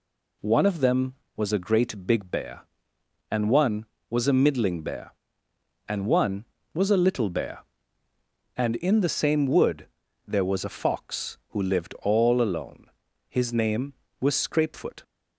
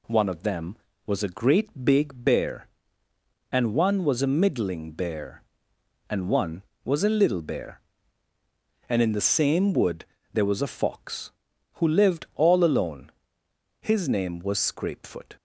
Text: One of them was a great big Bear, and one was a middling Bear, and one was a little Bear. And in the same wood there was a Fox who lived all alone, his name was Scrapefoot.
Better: neither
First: pauses between "wood" and "there"; at 9.8 s; 0.40 s long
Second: pauses between "wood" and "there"; slight; at 10.0 s; 0.30 s long

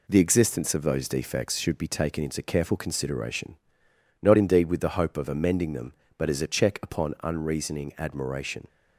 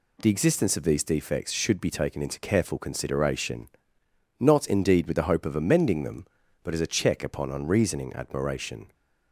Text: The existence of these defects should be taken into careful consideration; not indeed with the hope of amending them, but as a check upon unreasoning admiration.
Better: second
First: says "those" for "these"; at 0.8 s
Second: none

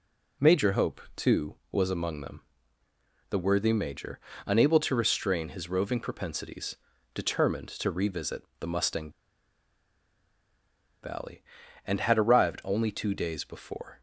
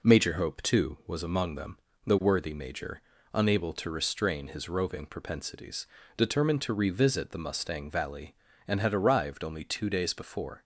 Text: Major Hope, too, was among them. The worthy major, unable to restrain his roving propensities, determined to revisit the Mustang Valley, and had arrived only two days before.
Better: second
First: pauses between "revisit" and "the"; slight; at 8.4 s; 0.16 s long // pauses between "Mustang" and "Valley"; strong; at 9.1 s; 1.9 s long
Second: none

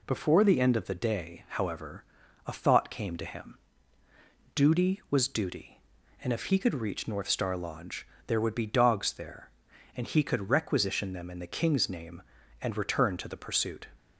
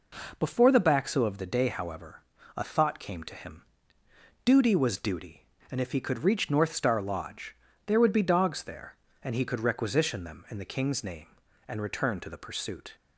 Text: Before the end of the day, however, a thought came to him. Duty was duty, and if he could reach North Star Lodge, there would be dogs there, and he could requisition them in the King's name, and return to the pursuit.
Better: first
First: none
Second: says "baxo" for "end"; at 0.8 s

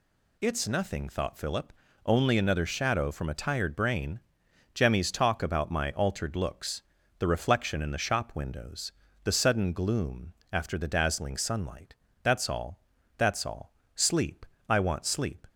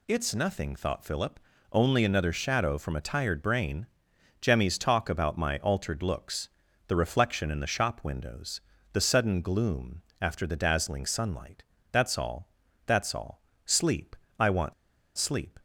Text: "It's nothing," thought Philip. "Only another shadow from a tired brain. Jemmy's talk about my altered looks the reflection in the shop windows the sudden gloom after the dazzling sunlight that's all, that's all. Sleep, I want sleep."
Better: first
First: pauses between "looks" and "the"; slight; at 6.8 s; 0.36 s long // pauses between "windows" and "the"; slight; at 8.9 s; 0.32 s long // pauses between "gloom" and "after"; slight; at 10.3 s; 0.18 s long // pauses between "sunlight" and "that's"; slight; at 11.9 s; 0.30 s long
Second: pauses between "looks" and "the"; at 6.4 s; 0.38 s long // pauses between "windows" and "the"; slight; at 8.6 s; 0.32 s long // pauses between "gloom" and "after"; slight; at 10.0 s; 0.18 s long // pauses between "sunlight" and "that's"; slight; at 11.6 s; 0.30 s long // pauses between "want" and "sleep"; at 14.7 s; 0.44 s long

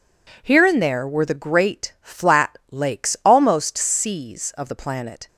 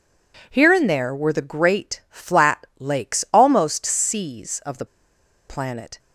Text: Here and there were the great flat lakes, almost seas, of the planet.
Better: first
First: none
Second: pauses between "the" and "planet"; noticeable; at 4.8 s; 0.63 s long

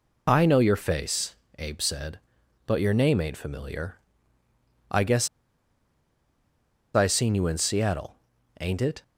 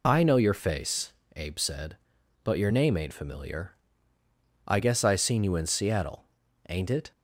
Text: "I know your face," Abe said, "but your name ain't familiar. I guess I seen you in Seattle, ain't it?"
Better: second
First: pauses between "guess" and "I"; strong; at 5.2 s; 1.6 s long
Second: none

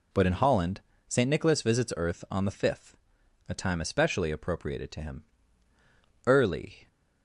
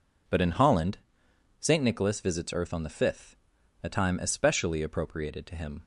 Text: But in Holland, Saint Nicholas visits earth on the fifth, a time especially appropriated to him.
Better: second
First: goes on to say "Early"; from 6.2 s on; 0.60 s long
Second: none

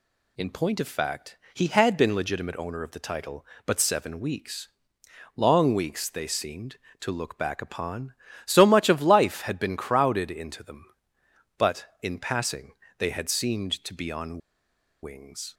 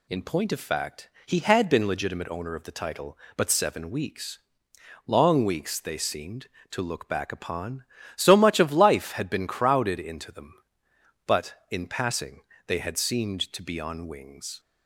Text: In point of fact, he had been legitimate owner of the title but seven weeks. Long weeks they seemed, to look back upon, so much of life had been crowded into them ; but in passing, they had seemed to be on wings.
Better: second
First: pauses between "on" and "wings"; noticeable; at 14.3 s; 0.65 s long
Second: none

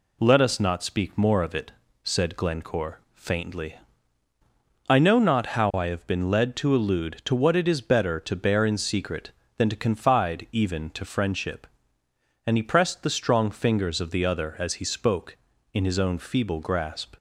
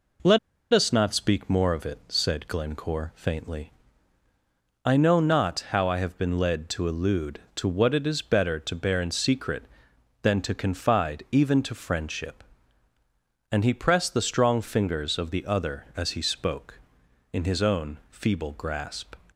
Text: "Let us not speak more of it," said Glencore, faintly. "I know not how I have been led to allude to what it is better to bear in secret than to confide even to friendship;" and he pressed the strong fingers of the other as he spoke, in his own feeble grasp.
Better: first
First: none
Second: pauses between "Let" and "us"; slight; at 0.3 s; 0.34 s long

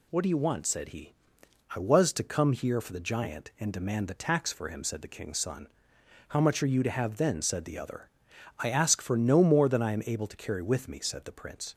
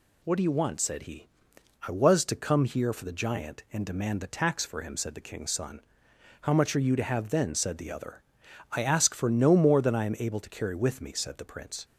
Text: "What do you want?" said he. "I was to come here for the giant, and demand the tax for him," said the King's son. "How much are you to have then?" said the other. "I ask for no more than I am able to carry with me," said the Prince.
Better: neither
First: none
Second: none

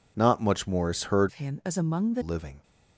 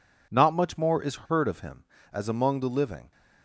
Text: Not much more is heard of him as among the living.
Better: second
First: changes voice from "of" to "the"; from 1.2 to 2.2 s; 1.0 s long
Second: none

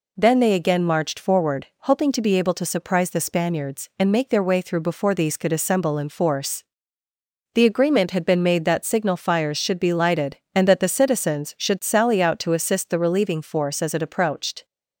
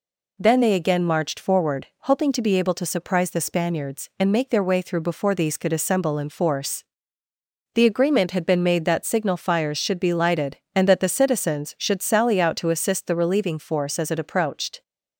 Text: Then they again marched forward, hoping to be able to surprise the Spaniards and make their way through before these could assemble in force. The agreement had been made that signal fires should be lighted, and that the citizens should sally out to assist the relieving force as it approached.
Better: neither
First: none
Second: none

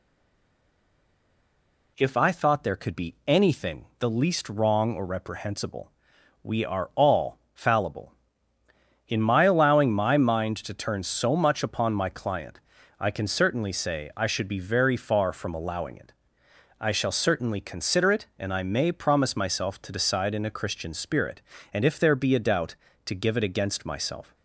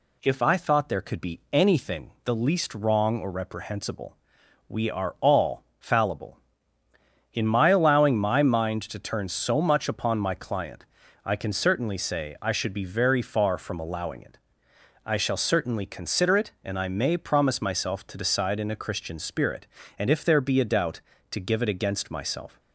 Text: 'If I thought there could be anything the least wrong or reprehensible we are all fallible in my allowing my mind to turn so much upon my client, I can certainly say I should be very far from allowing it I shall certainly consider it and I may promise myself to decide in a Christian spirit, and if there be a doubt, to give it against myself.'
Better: second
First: stays silent before the first word; noticeable; until 1.9 s; 1.9 s long // pauses between "anything" and "the"; slight; at 3.8 s; 0.16 s long // pauses between "reprehensible" and "we"; noticeable; at 5.9 s; 0.50 s long // pauses between "all" and "fallible"; slight; at 7.3 s; 0.16 s long // pauses between "it" and "I"; noticeable; at 16.1 s; 0.68 s long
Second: pauses between "anything" and "the"; slight; at 2.0 s; 0.16 s long // pauses between "reprehensible" and "we"; noticeable; at 4.1 s; 0.50 s long // pauses between "all" and "fallible"; slight; at 5.6 s; 0.16 s long // pauses between "it" and "I"; noticeable; at 14.3 s; 0.68 s long

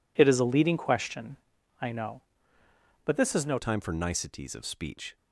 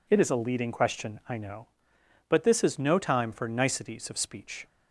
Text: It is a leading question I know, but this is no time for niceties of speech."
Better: second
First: pauses between "question" and "I"; at 1.3 s; 0.42 s long // changes voice at "time"; from 3.5 s on; 1.6 s long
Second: none

